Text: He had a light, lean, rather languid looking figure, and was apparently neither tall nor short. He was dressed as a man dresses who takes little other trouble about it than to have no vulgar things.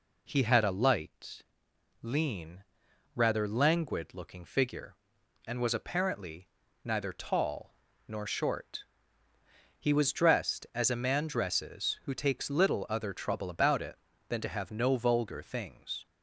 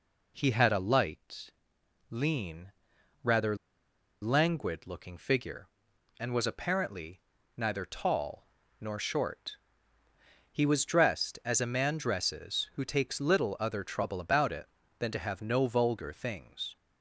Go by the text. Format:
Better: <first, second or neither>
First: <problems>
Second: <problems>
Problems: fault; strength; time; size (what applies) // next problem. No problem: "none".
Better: first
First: pauses between "apparently" and "neither"; slight; at 6.4 s; 0.34 s long // pauses between "tall" and "nor"; slight; at 7.7 s; 0.32 s long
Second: pauses between "rather" and "languid"; noticeable; at 3.5 s; 0.66 s long // pauses between "apparently" and "neither"; slight; at 7.2 s; 0.34 s long // pauses between "tall" and "nor"; slight; at 8.4 s; 0.32 s long